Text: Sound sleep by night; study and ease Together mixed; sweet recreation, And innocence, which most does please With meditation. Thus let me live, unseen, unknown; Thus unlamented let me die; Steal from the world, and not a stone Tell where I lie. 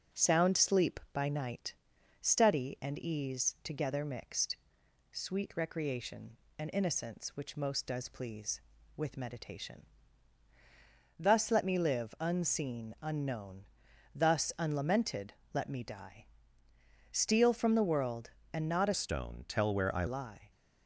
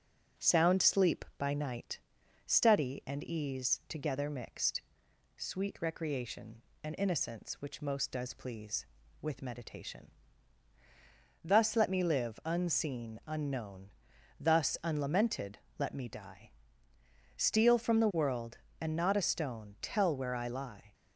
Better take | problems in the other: second | starts louder than the rest; noticeable; until 1.2 s; 6 dB; noticeable in the second // pauses between "unlamented" and "let"; slight; at 15.3 s; 0.22 s long; slight in the second // changes voice from "stone" to "I"; from 18.9 to 20.0 s; 1.1 s long

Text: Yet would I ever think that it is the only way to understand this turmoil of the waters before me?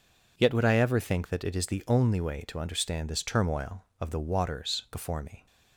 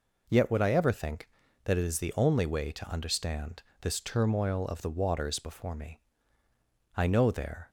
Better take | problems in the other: first | pauses between "understand" and "this"; slight; at 3.6 s; 0.18 s long // goes on to say "I know there"; noticeable; from 6.9 s on; 0.74 s long

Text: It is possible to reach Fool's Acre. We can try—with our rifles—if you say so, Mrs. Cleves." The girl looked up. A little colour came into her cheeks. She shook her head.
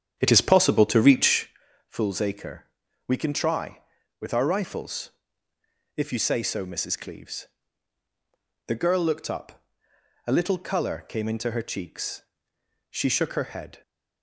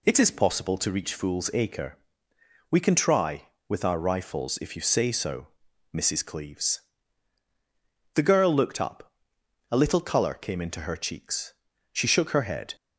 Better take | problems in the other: second | starts louder than the rest; strong; until 1.7 s; 8.5 dB // pauses between "reach" and "Fool's"; at 1.4 s; 0.38 s long

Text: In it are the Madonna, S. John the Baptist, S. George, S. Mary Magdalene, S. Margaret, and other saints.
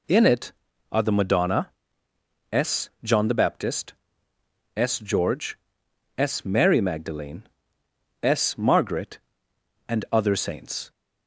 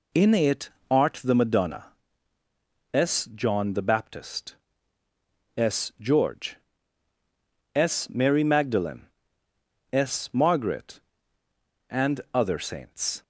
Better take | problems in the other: first | says "art" for "are"; at 0.9 s

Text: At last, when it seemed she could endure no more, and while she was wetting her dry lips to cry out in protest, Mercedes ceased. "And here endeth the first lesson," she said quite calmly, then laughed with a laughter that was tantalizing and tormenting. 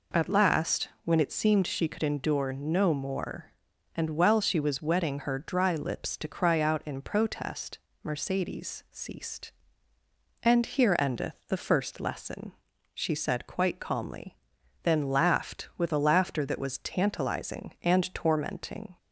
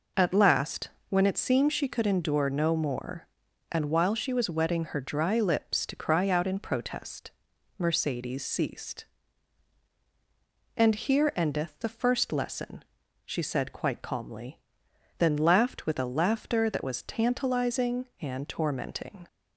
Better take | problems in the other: neither | none

